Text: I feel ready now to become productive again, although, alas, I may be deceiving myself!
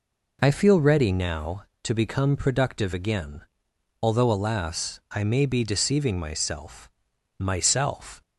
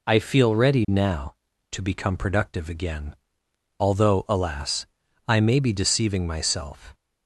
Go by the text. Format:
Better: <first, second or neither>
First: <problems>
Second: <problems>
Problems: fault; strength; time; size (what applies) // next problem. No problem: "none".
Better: second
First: says "myself" twice; at 7.3 s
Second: none